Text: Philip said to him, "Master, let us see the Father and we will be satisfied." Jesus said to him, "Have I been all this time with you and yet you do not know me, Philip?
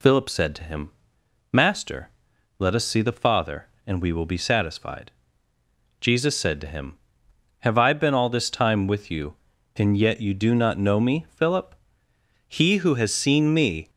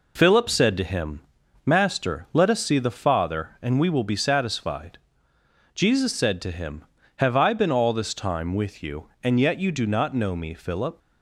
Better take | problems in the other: second | goes on to say "He who has seen me"; from 12.4 s on; 1.4 s long

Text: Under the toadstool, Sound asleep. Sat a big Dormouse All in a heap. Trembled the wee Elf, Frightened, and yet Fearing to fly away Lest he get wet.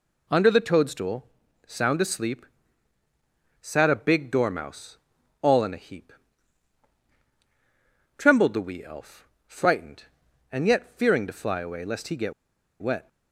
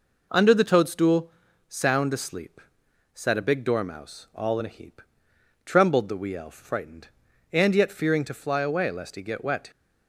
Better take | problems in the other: second | pauses between "Dormouse" and "All"; at 4.9 s; 0.44 s long // pauses between "get" and "wet"; noticeable; at 12.3 s; 0.48 s long

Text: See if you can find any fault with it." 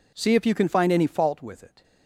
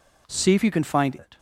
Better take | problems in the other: first | skips "any fault with"; at 1.1 s

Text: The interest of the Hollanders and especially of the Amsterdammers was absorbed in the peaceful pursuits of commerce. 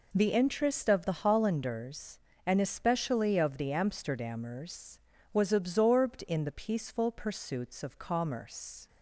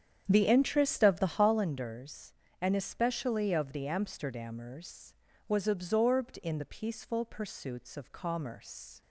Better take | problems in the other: first | starts louder than the rest; strong; until 1.5 s; 8.5 dB

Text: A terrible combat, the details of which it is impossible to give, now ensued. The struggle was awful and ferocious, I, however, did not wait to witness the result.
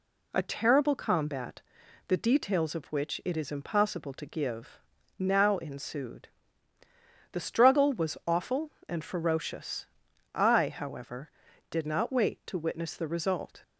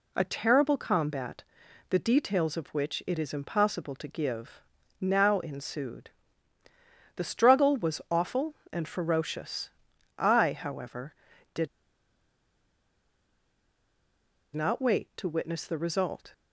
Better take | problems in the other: first | pauses between "did" and "not"; strong; at 11.6 s; 2.8 s long

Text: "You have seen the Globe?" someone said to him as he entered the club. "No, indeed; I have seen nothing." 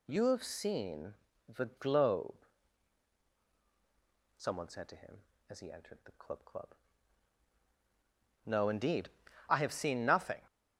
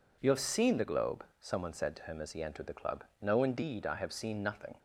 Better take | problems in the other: second | pauses between "seen" and "the"; slight; at 1.1 s; 0.34 s long // says "club" twice; at 6.4 s

